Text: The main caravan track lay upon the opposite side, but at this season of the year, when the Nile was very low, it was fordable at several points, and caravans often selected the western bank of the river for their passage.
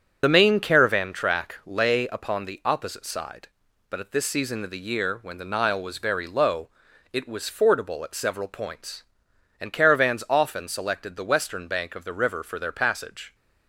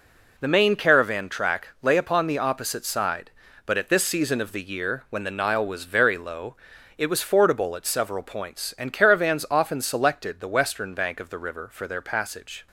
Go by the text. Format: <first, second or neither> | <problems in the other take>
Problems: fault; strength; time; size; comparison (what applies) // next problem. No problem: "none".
second | loses the start of "The"; at 0.2 s; 45 ms // starts louder than the rest; strong; until 1.2 s; 7.5 dB